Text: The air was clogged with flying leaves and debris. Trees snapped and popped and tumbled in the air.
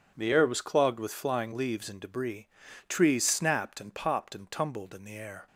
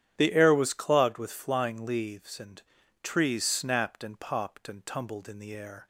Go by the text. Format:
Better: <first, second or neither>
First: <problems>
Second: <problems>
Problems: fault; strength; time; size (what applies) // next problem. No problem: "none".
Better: first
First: none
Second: starts louder than the rest; strong; until 1.1 s; 10.5 dB // skips "debris"; at 2.8 s